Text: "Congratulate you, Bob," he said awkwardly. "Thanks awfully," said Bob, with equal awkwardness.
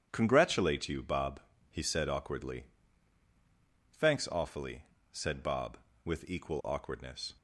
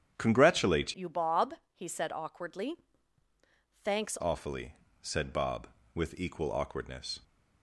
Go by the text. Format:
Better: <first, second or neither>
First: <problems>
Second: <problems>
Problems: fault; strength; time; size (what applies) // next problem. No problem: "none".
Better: first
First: starts louder than the rest; strong; until 1.1 s; 9 dB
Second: starts louder than the rest; strong; until 1.1 s; 9 dB // changes voice from "you" to "Thanks"; from 0.9 to 4.1 s; 3.2 s long